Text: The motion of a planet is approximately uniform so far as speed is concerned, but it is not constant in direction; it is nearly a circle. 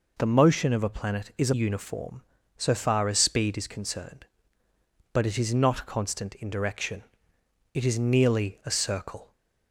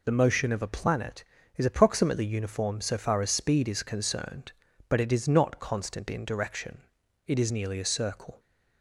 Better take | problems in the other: second | skips "approximately"; at 1.5 s

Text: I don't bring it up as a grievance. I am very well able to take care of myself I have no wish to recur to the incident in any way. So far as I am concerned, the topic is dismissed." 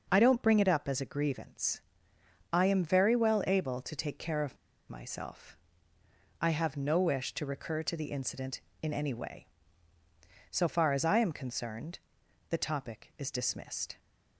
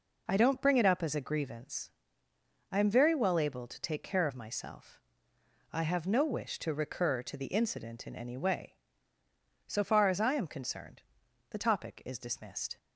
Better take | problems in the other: second | pauses between "of" and "myself"; slight; at 4.5 s; 0.32 s long // pauses between "myself" and "I"; noticeable; at 5.5 s; 0.86 s long; noticeable in the second

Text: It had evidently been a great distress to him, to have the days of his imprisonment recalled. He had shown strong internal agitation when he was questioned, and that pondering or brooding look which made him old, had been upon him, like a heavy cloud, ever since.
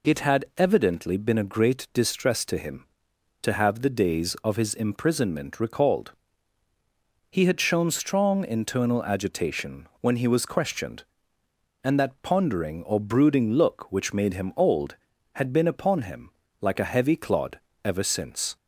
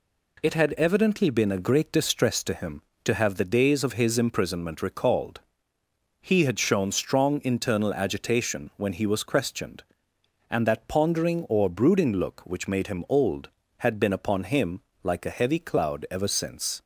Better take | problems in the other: second | says "clod" for "cloud"; at 17.1 s

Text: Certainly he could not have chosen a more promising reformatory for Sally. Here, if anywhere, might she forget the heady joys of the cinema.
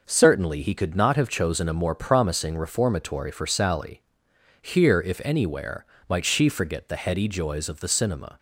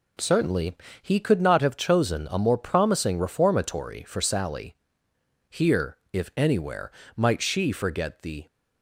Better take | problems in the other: first | pauses between "Certainly" and "he"; slight; at 0.7 s; 0.28 s long // stops before "heady joys of the cinema"; at 8.4 s

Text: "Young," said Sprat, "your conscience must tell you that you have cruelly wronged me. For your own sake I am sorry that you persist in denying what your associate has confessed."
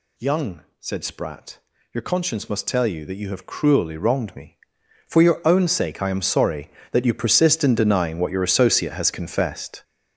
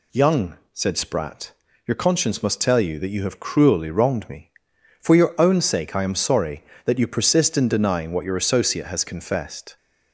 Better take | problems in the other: second | gets louder; strong; throughout; 9 dB

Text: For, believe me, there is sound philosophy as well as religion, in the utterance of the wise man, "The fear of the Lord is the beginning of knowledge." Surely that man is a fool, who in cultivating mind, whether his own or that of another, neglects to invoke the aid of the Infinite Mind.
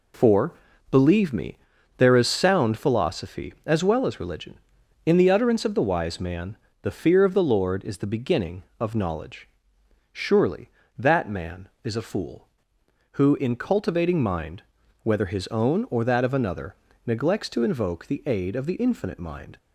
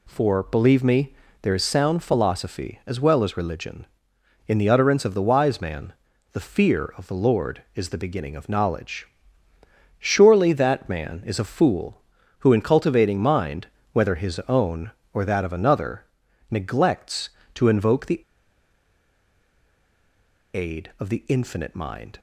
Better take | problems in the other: first | pauses between "the" and "aid"; strong; at 18.2 s; 2.3 s long

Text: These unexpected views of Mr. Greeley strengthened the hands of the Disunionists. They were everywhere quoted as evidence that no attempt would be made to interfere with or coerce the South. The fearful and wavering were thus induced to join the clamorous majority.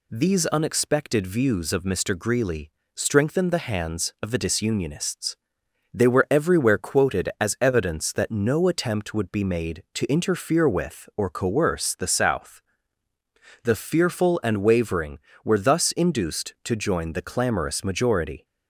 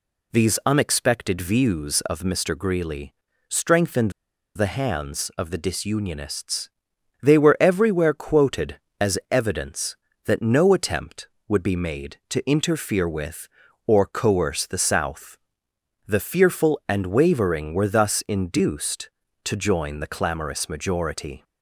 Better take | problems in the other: first | pauses between "Greeley" and "strengthened"; slight; at 3.1 s; 0.34 s long; slight in the first // pauses between "strengthened" and "the"; at 4.0 s; 0.45 s long

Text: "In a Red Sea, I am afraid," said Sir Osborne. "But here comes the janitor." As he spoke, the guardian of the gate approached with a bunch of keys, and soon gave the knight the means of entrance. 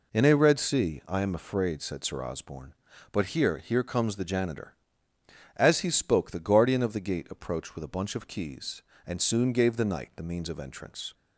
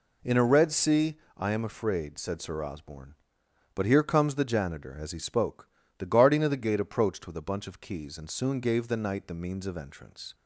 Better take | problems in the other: second | says "here" twice; at 3.5 s

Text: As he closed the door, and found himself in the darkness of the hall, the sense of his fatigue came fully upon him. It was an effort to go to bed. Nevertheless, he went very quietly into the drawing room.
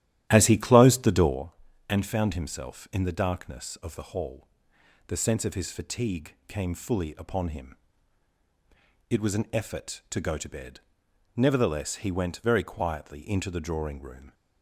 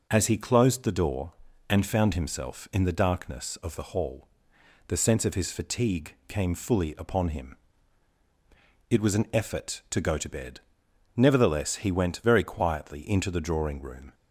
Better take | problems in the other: second | starts louder than the rest; strong; until 1.4 s; 12.5 dB

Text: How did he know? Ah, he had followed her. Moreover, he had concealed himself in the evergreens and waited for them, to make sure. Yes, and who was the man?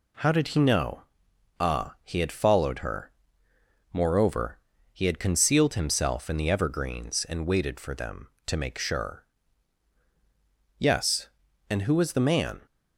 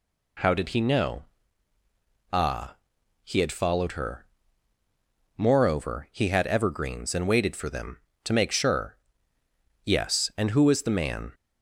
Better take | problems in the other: first | skips "concealed himself in the"; at 6.4 s

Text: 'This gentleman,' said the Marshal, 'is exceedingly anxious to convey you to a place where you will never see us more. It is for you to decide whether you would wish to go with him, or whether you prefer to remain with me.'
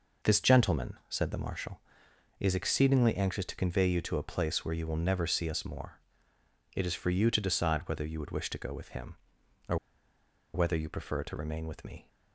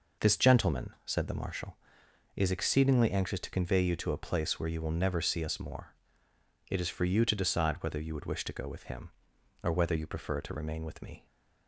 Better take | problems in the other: second | pauses between "or" and "whether"; noticeable; at 9.7 s; 0.78 s long

